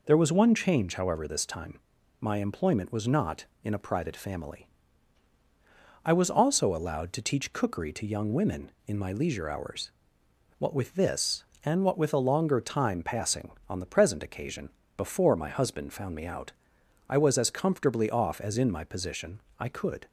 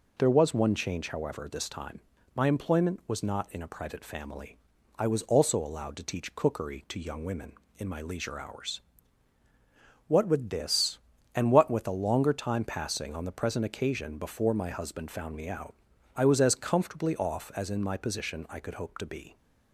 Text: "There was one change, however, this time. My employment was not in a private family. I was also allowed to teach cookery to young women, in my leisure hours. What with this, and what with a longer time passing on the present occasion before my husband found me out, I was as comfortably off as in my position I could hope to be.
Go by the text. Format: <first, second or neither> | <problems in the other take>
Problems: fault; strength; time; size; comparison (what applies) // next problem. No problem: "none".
second | pauses between "occasion" and "before"; slight; at 14.6 s; 0.28 s long // pauses between "position" and "I"; slight; at 19.4 s; 0.18 s long // stops before "hope to be"; at 20.0 s